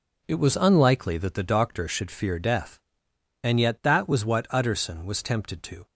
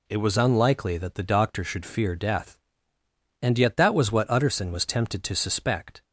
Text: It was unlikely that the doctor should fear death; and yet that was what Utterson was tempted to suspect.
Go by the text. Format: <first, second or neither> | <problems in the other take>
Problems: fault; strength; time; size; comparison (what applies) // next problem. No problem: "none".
second | stops before "suspect"; at 5.8 s